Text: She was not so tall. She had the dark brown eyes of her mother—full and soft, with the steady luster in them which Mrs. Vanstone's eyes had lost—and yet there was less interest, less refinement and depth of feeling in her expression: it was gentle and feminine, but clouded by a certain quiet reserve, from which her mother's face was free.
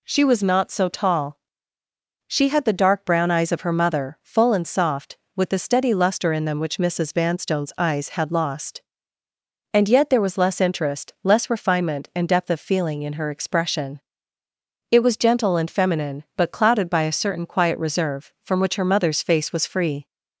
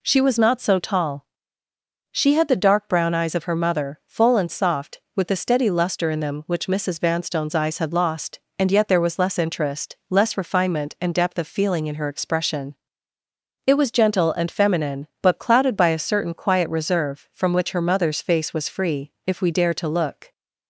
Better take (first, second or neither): first